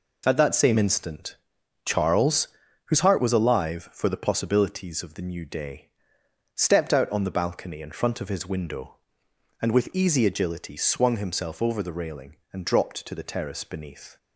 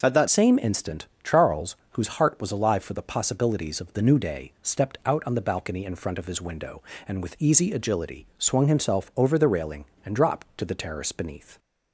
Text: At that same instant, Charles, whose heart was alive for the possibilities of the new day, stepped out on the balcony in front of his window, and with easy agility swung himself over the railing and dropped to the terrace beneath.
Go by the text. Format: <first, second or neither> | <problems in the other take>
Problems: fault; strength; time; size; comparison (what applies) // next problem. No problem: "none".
first | changes voice at "same"; from 0.2 s on; 11.3 s long